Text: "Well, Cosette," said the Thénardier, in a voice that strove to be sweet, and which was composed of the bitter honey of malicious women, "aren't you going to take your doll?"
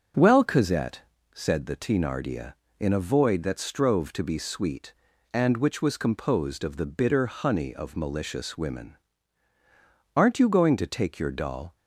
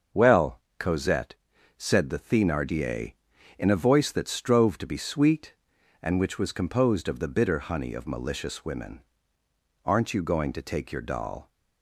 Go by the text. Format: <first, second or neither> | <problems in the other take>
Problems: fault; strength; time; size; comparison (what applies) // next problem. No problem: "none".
second | starts louder than the rest; noticeable; until 1.4 s; 6 dB; also in the second // says "void" for "voice"; at 3.0 s